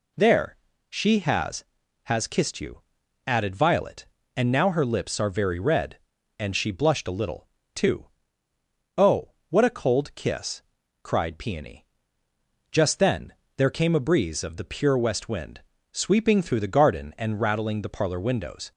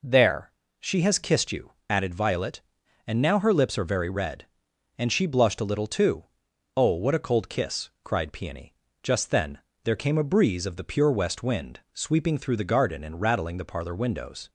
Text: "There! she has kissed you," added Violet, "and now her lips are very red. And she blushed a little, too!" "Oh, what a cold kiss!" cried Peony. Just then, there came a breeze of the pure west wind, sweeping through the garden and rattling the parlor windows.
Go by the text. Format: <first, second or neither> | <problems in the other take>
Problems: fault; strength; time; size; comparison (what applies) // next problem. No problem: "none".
second | says "has" twice; at 2.0 s